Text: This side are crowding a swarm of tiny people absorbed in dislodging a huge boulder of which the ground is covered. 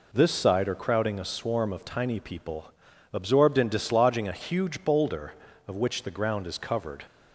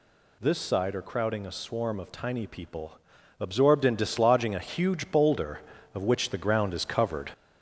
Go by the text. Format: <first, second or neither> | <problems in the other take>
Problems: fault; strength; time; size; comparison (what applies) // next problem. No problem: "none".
first | gets louder; throughout; 3.5 dB // pauses between "people" and "absorbed"; at 2.9 s; 0.44 s long; also in the first